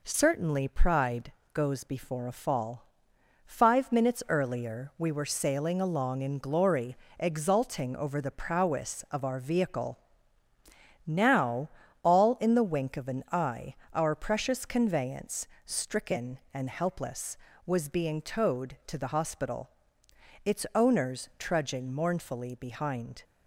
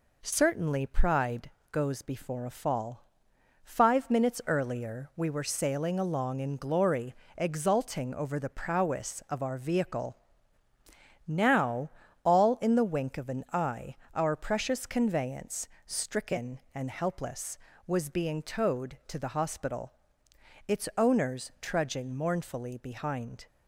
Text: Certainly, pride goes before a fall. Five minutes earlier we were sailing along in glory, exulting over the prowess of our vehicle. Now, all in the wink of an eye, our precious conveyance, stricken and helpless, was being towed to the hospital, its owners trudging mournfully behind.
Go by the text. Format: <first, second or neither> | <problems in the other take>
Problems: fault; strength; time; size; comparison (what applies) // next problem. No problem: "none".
neither | pauses between "pride" and "goes"; slight; the same in both